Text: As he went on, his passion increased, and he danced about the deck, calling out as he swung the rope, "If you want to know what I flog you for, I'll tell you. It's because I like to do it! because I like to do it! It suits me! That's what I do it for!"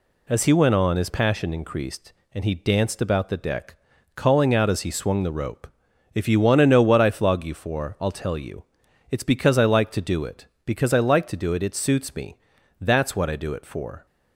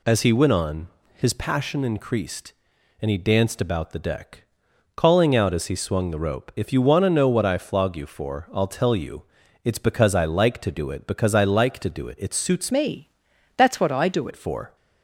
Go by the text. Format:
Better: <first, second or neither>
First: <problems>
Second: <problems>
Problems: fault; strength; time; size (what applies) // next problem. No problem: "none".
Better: first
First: none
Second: changes voice from "me" to "do"; from 12.7 to 14.2 s; 1.5 s long